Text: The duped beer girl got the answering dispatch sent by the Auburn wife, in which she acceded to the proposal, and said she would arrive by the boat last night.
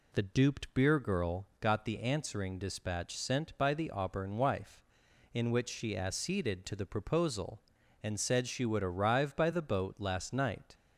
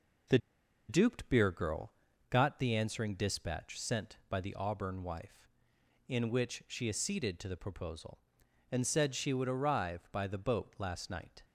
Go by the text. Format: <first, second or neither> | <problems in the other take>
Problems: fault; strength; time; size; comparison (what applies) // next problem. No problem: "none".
first | pauses between "The" and "duped"; noticeable; at 0.3 s; 0.51 s long // pauses between "girl" and "got"; slight; at 1.9 s; 0.34 s long